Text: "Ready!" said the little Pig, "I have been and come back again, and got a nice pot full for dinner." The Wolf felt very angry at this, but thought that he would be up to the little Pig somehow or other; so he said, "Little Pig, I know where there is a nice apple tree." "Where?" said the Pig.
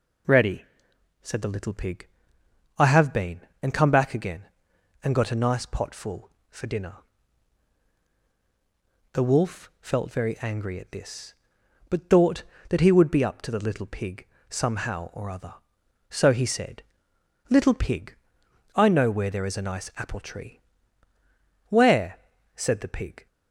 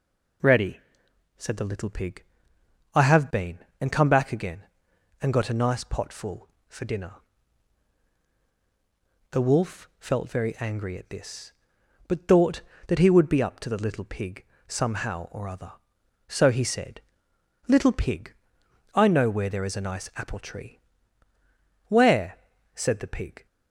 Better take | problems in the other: neither | pauses between "Pig" and "somehow"; slight; the same in both

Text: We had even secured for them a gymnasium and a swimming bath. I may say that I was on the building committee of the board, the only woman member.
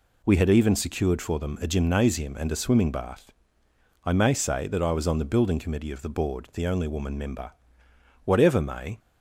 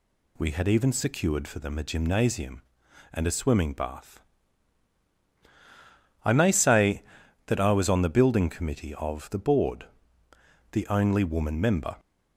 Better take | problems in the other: second | goes on to say "Whatever may"; noticeable; from 8.2 s on; 0.74 s long

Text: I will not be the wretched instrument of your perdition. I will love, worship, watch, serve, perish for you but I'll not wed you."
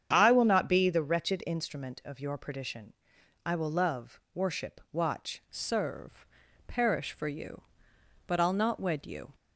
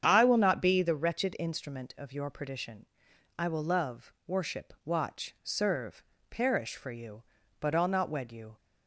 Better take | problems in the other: second | starts louder than the rest; strong; until 1.1 s; 8.5 dB; strong in the second // changes voice at "serve"; from 5.5 s on; 3.8 s long

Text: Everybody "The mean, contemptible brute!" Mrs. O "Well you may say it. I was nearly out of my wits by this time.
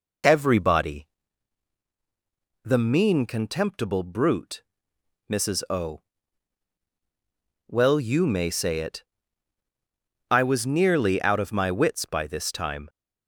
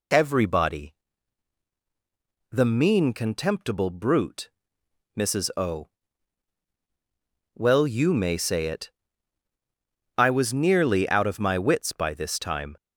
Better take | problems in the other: second | starts louder than the rest; noticeable; until 1.3 s; 4 dB // pauses between "Everybody" and "The"; strong; at 1.0 s; 1.5 s long; strong in the second // pauses between "O" and "Well"; strong; at 6.0 s; 1.6 s long; strong in the second

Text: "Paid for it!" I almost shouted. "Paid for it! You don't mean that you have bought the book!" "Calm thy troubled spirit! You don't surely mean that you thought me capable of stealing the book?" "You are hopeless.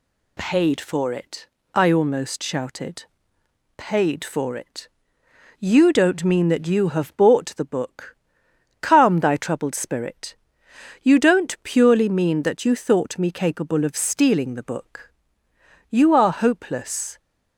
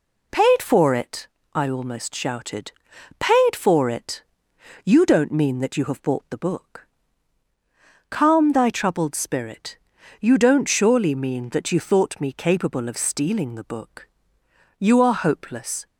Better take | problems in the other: second | says "purely" for "surely"; at 11.6 s

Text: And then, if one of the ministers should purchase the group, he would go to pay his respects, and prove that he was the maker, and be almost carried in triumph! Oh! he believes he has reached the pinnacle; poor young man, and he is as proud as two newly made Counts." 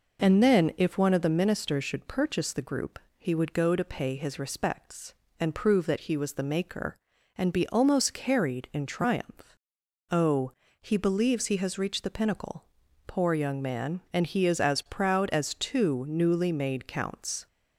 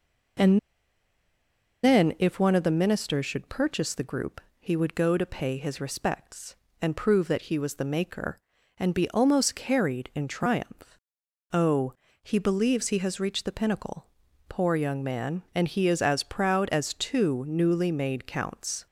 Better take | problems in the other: first | pauses between "And" and "then"; strong; at 0.5 s; 1.2 s long

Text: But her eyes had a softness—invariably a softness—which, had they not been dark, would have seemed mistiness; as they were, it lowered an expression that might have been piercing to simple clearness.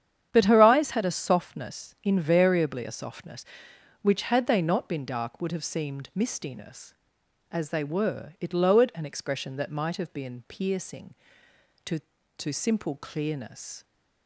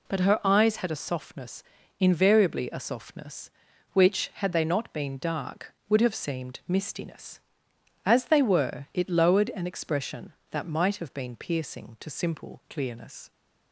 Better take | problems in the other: second | starts louder than the rest; strong; until 1.3 s; 9 dB // says "to" twice; at 12.3 s

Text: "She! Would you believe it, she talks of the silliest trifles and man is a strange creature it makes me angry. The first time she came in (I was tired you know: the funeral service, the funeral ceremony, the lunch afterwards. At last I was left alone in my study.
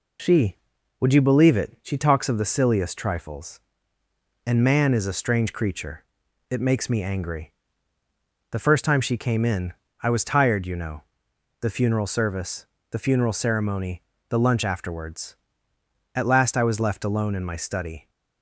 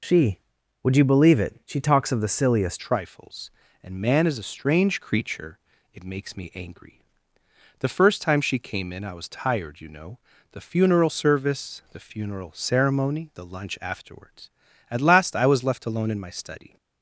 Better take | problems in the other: first | changes voice at "trifles"; from 2.7 s on; 14.0 s long // pauses between "creature" and "it"; slight; at 5.5 s; 0.36 s long; noticeable in the first

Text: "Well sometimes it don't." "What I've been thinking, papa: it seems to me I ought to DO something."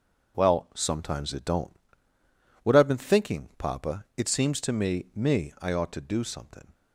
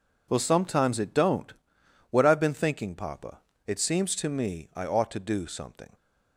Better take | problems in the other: second | starts louder than the rest; noticeable; until 1.4 s; 6 dB // says "me" twice; at 5.1 s

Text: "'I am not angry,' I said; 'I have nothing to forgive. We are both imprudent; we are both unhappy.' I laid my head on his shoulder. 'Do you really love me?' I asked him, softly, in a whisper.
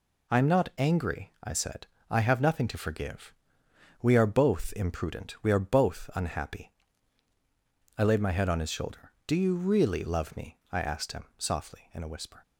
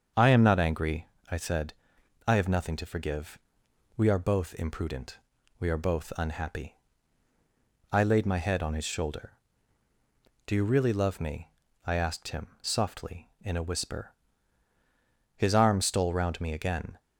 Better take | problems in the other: first | starts louder than the rest; until 1.4 s; 6.5 dB // goes on to say "His arm stole round me again"; from 15.3 s on; 1.6 s long

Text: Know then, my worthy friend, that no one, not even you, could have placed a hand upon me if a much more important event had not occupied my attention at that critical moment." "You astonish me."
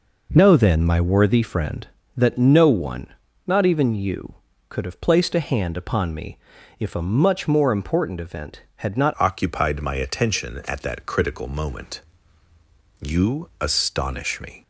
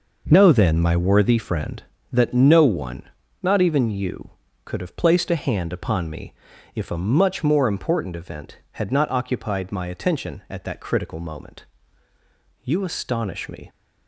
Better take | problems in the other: second | pauses between "me" and "if"; at 6.3 s; 0.42 s long; also in the second // changes voice at "occupied"; from 9.1 s on; 5.5 s long

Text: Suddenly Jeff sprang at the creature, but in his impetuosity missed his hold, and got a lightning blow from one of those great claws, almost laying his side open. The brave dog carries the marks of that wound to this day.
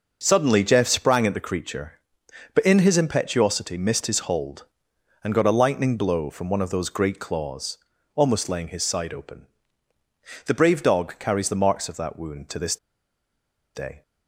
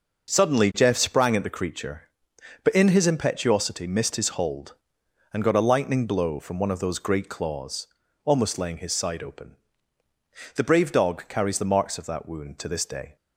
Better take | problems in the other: second | pauses between "this" and "day"; at 12.7 s; 0.99 s long

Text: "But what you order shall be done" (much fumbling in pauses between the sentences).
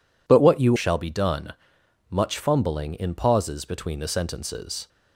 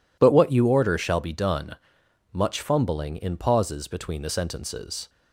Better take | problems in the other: second | skips "order"; at 0.7 s

